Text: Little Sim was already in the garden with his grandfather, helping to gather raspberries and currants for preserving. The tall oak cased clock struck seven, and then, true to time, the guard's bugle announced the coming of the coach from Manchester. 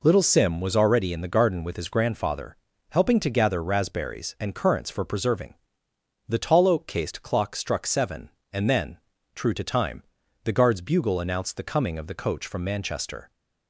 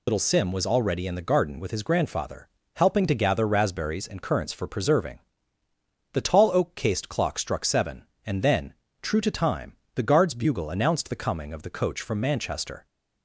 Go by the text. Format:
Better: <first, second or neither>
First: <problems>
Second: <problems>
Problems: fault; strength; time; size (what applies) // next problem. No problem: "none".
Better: first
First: none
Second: loses the start of "Little"; at 0.0 s; 95 ms